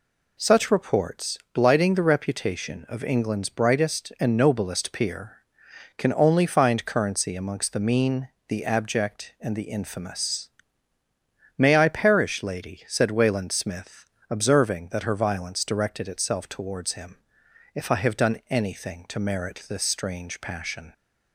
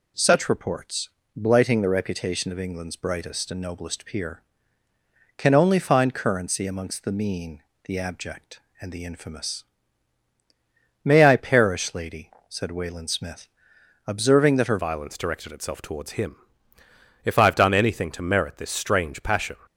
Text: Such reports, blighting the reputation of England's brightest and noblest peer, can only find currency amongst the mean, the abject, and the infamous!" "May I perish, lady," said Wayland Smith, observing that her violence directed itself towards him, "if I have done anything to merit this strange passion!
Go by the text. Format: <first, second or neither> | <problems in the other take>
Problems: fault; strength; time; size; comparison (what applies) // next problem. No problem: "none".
first | changes voice at "violence"; from 14.7 s on; 4.8 s long